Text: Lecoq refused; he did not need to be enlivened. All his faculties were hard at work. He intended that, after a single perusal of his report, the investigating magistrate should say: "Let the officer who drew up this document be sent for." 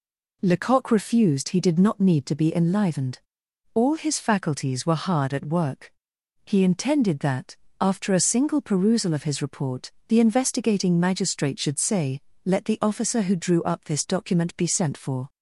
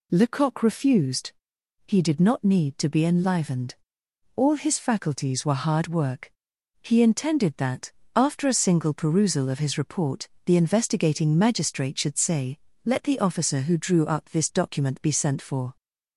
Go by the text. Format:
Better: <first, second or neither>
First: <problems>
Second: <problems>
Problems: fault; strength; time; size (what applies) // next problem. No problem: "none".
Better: first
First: none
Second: skips "at"; at 5.8 s